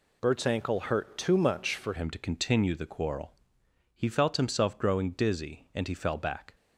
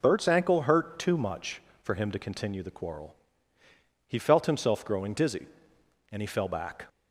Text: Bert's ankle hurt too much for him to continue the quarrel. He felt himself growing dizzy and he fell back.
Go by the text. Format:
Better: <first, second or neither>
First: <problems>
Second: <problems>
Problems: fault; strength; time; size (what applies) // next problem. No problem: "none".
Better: second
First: changes voice at "him"; from 1.9 s on; 4.6 s long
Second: none